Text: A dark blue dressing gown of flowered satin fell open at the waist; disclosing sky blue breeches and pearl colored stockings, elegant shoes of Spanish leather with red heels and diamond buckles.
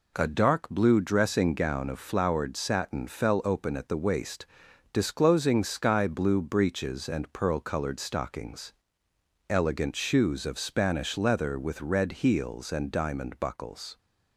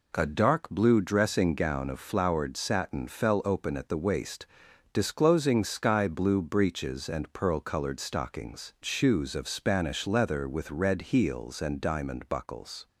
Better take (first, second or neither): first